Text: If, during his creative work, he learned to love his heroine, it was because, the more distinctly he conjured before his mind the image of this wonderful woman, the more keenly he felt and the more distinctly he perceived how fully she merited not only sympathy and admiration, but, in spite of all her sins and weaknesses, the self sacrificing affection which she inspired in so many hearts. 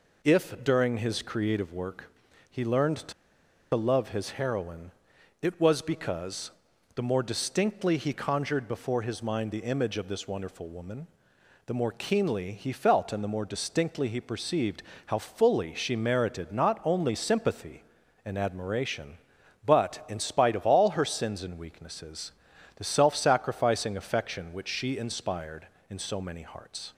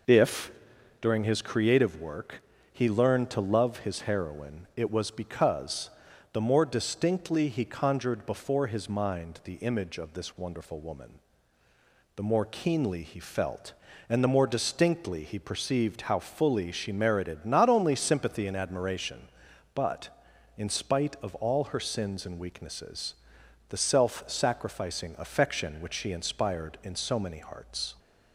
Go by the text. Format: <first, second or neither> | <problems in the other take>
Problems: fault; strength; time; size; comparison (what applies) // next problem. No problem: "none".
second | pauses between "to" and "love"; noticeable; at 3.1 s; 0.61 s long // pauses between "perceived" and "how"; slight; at 14.8 s; 0.26 s long